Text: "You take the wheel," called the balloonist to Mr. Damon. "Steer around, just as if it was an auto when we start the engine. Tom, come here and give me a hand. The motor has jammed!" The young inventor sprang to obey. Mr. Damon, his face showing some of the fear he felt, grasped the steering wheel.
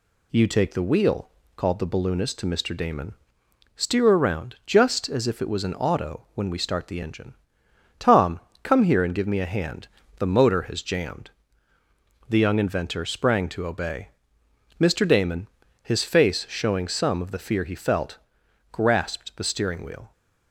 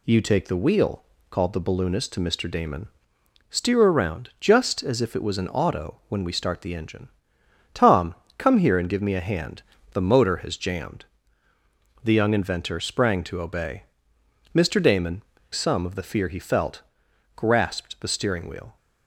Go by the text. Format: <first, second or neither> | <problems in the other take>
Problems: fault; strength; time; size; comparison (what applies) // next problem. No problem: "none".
first | skips "his face showing"; at 15.3 s